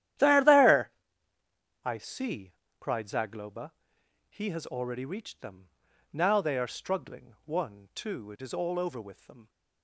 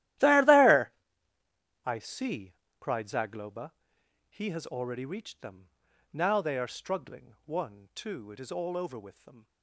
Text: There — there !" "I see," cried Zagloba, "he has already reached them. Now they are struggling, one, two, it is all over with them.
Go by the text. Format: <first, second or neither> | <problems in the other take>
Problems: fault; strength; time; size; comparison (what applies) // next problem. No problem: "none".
first | gets quieter; noticeable; throughout; 5 dB // starts louder than the rest; strong; until 1.6 s; 14 dB; strong in the first